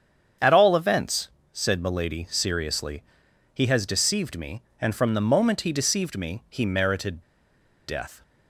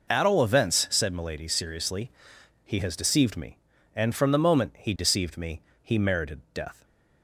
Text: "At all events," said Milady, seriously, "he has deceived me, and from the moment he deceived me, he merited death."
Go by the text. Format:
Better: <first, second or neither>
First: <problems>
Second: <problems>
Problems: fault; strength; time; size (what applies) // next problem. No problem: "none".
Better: second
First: starts louder than the rest; strong; until 1.6 s; 8 dB // pauses between "merited" and "death"; noticeable; at 7.2 s; 0.66 s long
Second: none